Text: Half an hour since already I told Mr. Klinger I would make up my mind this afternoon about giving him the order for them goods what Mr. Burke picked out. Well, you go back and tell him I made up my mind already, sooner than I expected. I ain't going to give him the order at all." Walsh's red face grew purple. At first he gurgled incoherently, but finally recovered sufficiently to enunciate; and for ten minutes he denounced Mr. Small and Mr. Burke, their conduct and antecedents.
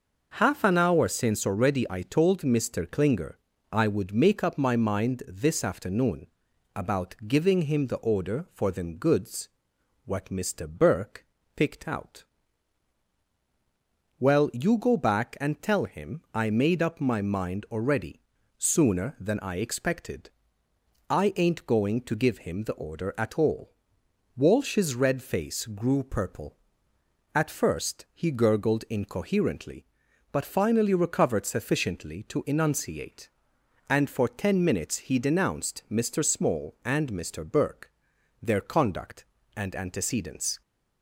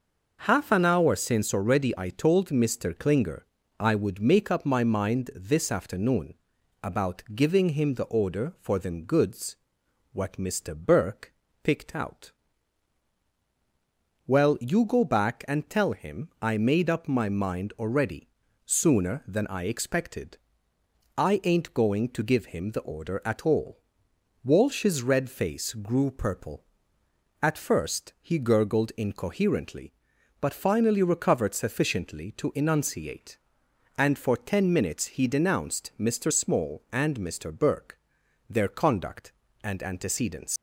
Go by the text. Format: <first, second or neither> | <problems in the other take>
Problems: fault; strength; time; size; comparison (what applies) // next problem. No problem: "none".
first | pauses between "Klinger" and "I"; slight; at 3.4 s; 0.34 s long; slight in the first // pauses between "afternoon" and "about"; noticeable; at 6.3 s; 0.48 s long; noticeable in the first // pauses between "goods" and "what"; noticeable; at 9.5 s; 0.56 s long; noticeable in the first // pauses between "Burke" and "picked"; slight; at 11.3 s; 0.28 s long; slight in the first // leaves "antecedents" unfinished; at 40.5 s; 125 ms